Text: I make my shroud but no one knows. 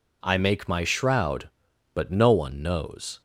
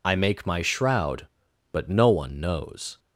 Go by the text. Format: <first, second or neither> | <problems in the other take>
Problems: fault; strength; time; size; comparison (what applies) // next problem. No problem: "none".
first | loses the start of "I"; at 0.0 s; 40 ms